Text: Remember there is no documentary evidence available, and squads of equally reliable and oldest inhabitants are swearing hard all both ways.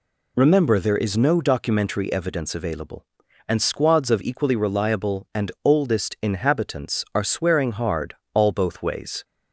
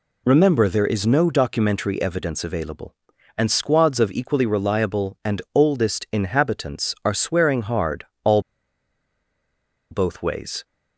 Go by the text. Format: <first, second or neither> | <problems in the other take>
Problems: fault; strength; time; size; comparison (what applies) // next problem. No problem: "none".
first | pauses between "hard" and "all"; slight; at 8.0 s; 0.18 s long; slight in the first // pauses between "all" and "both"; strong; at 8.3 s; 1.5 s long